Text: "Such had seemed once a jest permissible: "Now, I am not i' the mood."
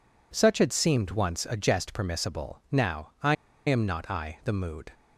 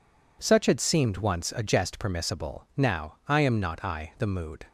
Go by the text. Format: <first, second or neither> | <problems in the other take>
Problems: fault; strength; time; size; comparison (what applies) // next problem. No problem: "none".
second | pauses between "I" and "am"; slight; at 3.3 s; 0.32 s long